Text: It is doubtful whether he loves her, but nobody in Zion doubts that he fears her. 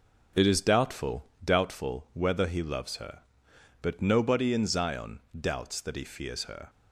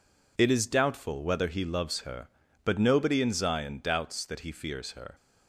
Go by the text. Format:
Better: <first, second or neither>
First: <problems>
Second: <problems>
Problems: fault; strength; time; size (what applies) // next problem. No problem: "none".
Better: second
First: says "doubtful" twice; at 1.4 s // pauses between "Zion" and "doubts"; slight; at 5.2 s; 0.17 s long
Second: none